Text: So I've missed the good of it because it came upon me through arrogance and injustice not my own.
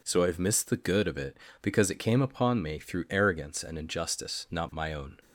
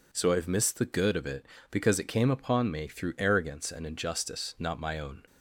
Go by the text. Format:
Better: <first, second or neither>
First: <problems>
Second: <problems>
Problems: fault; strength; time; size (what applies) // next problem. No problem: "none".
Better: neither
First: none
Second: none